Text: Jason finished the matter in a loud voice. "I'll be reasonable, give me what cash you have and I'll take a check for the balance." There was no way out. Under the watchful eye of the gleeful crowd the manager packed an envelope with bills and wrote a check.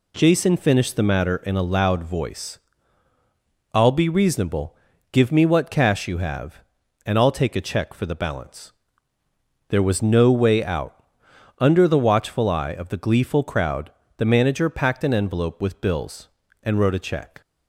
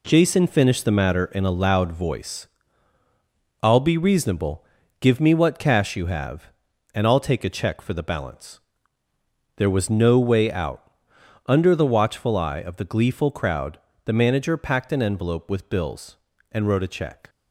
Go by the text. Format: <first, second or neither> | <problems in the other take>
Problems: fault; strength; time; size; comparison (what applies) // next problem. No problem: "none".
first | gets quieter; strong; throughout; 8 dB // pauses between "crowd" and "the"; slight; at 13.7 s; 0.24 s long; slight in the first